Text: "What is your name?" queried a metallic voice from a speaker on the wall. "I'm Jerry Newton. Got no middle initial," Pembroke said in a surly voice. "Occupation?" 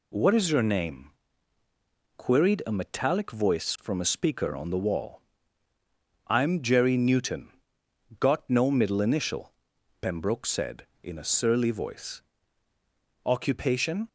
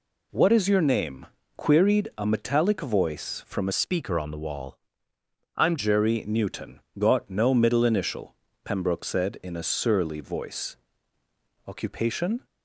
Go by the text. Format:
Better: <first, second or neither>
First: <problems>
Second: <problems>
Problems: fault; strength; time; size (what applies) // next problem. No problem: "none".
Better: first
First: none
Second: changes voice from "speaker" to "I'm"; from 3.7 to 5.7 s; 2.0 s long